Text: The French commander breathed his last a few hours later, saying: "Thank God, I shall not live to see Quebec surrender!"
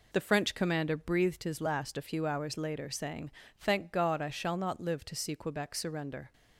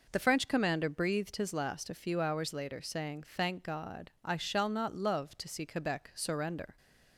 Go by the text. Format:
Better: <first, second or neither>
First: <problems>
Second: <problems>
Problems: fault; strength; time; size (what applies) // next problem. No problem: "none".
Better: first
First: none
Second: says "love" for "live"; at 4.9 s